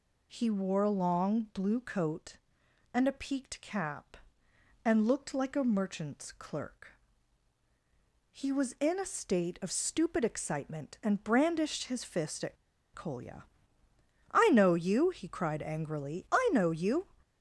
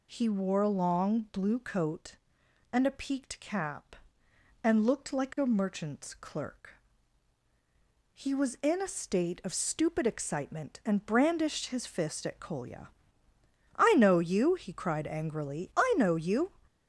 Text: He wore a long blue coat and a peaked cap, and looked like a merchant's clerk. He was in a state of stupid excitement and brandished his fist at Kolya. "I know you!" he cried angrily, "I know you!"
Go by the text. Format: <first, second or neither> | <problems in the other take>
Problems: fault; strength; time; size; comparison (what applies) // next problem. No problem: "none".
second | pauses between "at" and "Kolya"; at 12.5 s; 0.37 s long